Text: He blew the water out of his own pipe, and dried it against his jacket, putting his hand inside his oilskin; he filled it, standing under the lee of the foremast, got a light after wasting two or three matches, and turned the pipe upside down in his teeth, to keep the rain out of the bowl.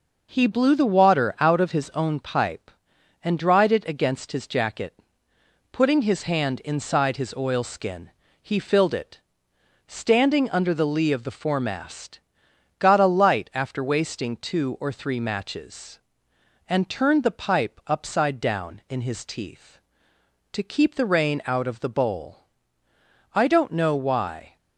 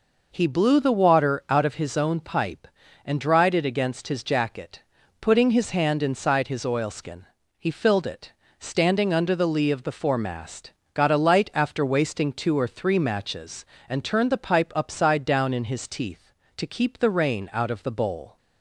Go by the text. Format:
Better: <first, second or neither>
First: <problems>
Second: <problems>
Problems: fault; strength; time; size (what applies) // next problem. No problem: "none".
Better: second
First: goes on to say "I don't know why"; noticeable; from 23.3 s on; 1.2 s long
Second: none